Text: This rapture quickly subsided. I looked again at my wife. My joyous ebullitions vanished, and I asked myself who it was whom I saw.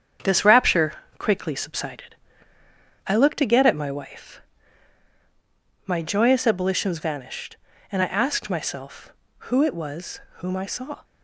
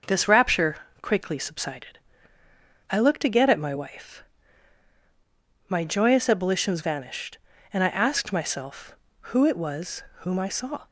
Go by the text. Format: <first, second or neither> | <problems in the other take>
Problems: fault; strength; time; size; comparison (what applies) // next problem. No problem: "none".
second | gets quieter; noticeable; throughout; 5 dB // starts louder than the rest; strong; until 1.4 s; 8 dB; noticeable in the second // pauses between "rapture" and "quickly"; slight; at 0.9 s; 0.24 s long; slight in the second // pauses between "was" and "whom"; slight; at 10.1 s; 0.18 s long; slight in the second